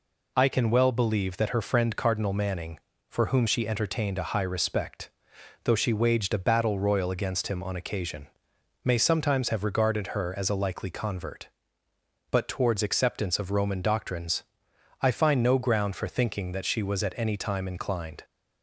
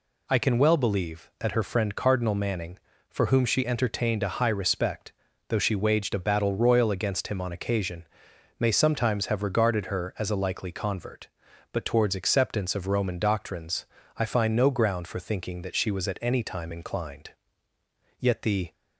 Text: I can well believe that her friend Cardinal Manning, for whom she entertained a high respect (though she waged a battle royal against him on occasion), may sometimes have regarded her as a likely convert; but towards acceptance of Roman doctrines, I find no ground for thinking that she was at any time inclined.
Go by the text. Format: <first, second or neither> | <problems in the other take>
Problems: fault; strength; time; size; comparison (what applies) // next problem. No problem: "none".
first | goes on to say "Yet the"; from 18.1 s on; 0.54 s long